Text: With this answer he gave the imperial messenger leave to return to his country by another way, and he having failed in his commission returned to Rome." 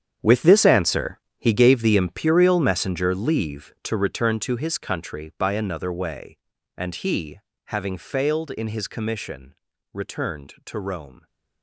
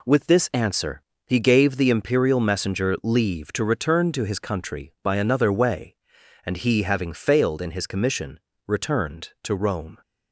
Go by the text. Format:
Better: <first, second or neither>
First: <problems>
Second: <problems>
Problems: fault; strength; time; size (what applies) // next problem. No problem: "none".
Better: second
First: gets quieter; strong; throughout; 13 dB // pauses between "answer" and "he"; slight; at 1.1 s; 0.20 s long // pauses between "he" and "having"; slight; at 7.3 s; 0.26 s long // pauses between "commission" and "returned"; at 9.5 s; 0.40 s long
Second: pauses between "answer" and "he"; slight; at 1.0 s; 0.26 s long // pauses between "commission" and "returned"; slight; at 8.3 s; 0.28 s long